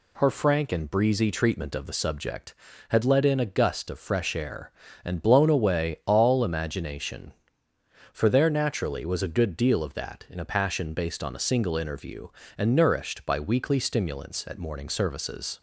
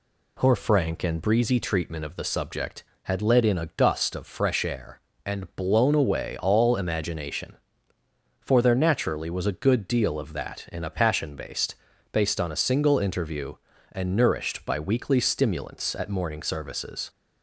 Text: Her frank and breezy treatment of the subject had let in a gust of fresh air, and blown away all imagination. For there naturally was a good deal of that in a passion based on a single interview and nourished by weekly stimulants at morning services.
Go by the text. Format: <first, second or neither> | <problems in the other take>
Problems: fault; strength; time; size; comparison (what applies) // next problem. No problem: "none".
first | says "based" twice; at 12.1 s